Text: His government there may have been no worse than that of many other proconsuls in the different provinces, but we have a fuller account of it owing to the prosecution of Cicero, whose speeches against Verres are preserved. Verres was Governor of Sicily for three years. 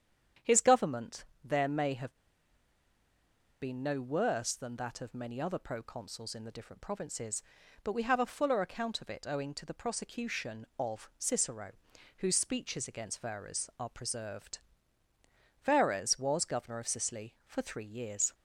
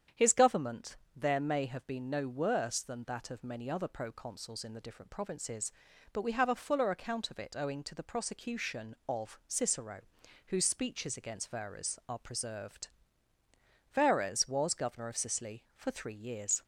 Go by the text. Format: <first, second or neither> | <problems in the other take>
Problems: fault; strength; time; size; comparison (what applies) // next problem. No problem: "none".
second | starts louder than the rest; strong; until 1.6 s; 8.5 dB; strong in the second // pauses between "government" and "there"; slight; at 1.2 s; 0.20 s long; slight in the second // pauses between "have" and "been"; strong; at 2.1 s; 1.4 s long